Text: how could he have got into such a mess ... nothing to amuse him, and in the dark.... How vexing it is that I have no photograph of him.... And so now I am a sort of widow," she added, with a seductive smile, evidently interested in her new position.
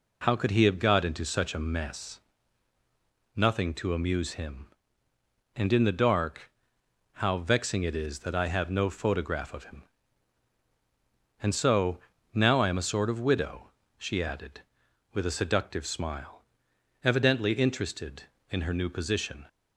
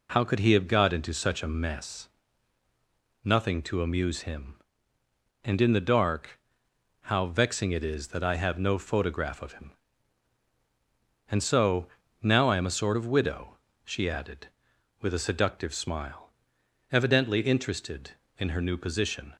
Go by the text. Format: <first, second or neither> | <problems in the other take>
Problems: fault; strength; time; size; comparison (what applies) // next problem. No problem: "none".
neither | pauses between "so" and "now"; slight; the same in both